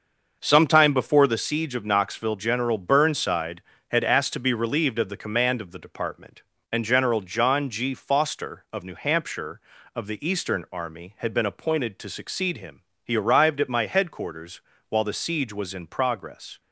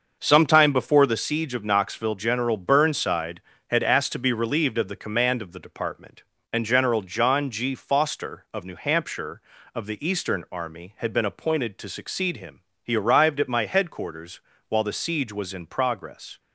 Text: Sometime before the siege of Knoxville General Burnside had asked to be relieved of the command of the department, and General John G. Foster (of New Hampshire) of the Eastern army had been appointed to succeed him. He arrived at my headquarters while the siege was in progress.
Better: neither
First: starts louder than the rest; until 1.4 s; 6.5 dB // pauses between "headquarters" and "while"; slight; at 14.5 s; 0.30 s long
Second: starts louder than the rest; until 1.2 s; 6.5 dB // pauses between "headquarters" and "while"; slight; at 14.3 s; 0.30 s long

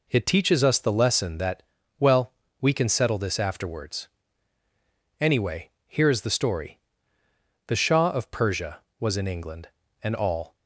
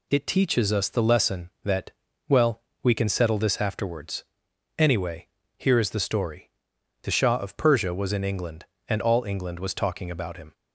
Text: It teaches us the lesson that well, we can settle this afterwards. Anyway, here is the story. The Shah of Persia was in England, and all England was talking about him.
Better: second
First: pauses between "that" and "well"; slight; at 1.6 s; 0.34 s long // stops before "England was talking about him"; at 10.5 s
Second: pauses between "that" and "well"; at 1.9 s; 0.38 s long

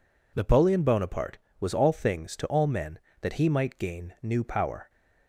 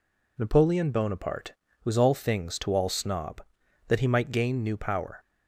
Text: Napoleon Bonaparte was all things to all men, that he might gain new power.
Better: first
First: none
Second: says "snob" for "men"; at 2.8 s

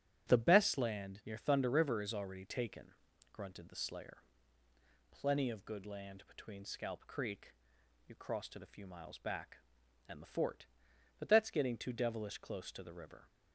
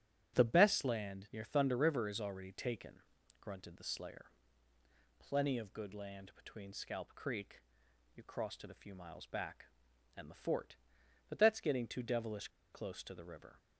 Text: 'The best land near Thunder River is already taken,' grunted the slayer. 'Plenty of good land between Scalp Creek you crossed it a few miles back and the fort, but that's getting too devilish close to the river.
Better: first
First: starts louder than the rest; strong; until 1.3 s; 11 dB // pauses between "Creek" and "you"; noticeable; at 7.5 s; 0.56 s long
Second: starts louder than the rest; strong; until 1.3 s; 11 dB // pauses between "Creek" and "you"; noticeable; at 7.6 s; 0.56 s long // pauses between "devilish" and "close"; slight; at 12.4 s; 0.23 s long

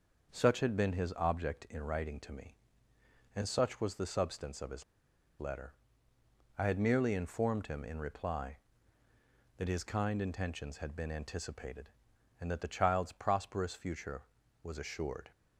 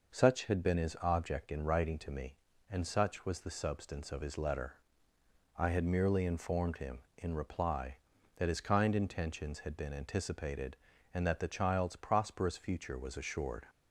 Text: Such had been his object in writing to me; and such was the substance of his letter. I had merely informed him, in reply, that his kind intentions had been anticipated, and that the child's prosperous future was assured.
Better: second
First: pauses between "his" and "letter"; noticeable; at 4.8 s; 0.57 s long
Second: none

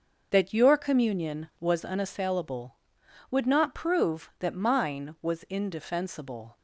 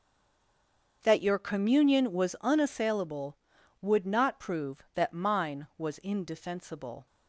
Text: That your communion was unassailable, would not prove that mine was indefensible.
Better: first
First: starts louder than the rest; until 1.3 s; 6.5 dB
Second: stays silent before the first word; until 1.0 s; 1.0 s long // starts louder than the rest; until 2.0 s; 6.5 dB

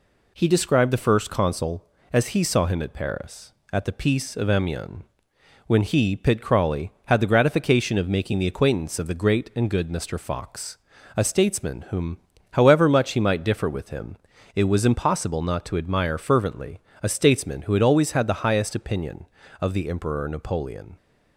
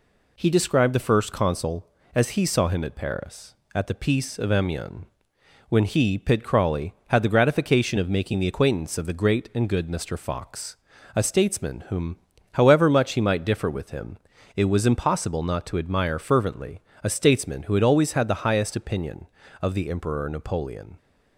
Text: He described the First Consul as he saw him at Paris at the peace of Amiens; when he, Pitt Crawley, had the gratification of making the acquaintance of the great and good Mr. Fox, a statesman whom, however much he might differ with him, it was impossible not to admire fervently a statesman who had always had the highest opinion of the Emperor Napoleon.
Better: neither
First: pauses between "fervently" and "a"; slight; at 16.7 s; 0.22 s long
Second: pauses between "fervently" and "a"; slight; at 16.8 s; 0.22 s long

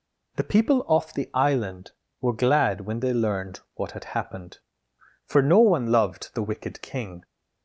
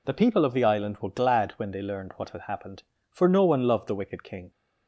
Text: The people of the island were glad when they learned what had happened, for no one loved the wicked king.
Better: second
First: says "off" for "of"; at 0.8 s // pauses between "learned" and "what"; slight; at 3.5 s; 0.16 s long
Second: none

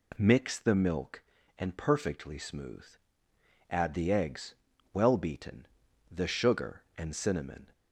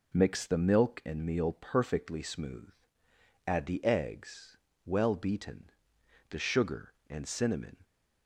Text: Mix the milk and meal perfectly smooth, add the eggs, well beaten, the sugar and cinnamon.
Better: second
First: skips "meal"; at 1.7 s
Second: none

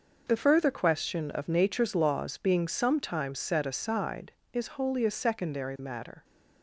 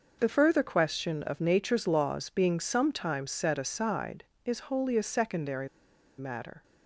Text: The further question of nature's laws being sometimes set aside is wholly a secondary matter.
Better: first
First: none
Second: pauses between "secondary" and "matter"; noticeable; at 5.6 s; 0.50 s long

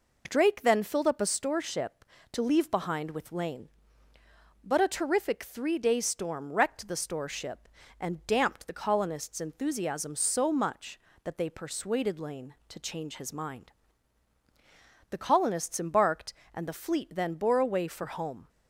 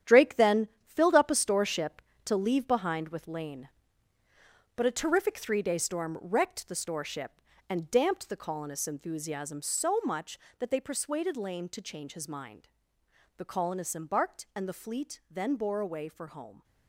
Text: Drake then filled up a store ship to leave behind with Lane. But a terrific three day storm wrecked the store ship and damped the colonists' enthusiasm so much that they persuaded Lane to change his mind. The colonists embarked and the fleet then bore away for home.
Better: first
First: none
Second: gets quieter; strong; throughout; 9.5 dB // pauses between "then" and "filled"; slight; at 0.6 s; 0.18 s long

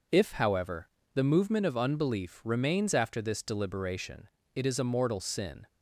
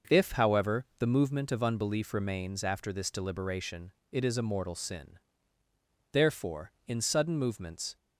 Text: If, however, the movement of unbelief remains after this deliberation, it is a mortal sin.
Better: first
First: none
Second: starts louder than the rest; noticeable; until 1.2 s; 6 dB // goes on to say "Therefore in sudden movements"; strong; from 6.1 s on; 1.8 s long

